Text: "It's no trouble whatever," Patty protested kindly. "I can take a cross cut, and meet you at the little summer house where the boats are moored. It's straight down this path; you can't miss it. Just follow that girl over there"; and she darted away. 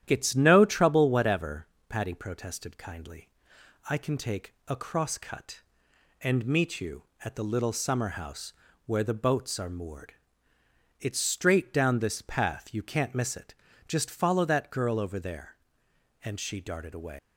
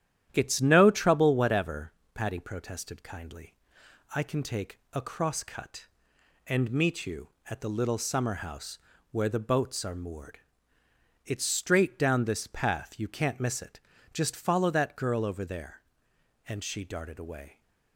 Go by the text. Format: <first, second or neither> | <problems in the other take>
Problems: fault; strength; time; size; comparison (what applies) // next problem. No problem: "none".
second | starts louder than the rest; strong; until 1.0 s; 11 dB; strong in the second // pauses between "house" and "where"; slight; at 8.5 s; 0.34 s long; slight in the second // leaves "away" unfinished; at 17.1 s; 170 ms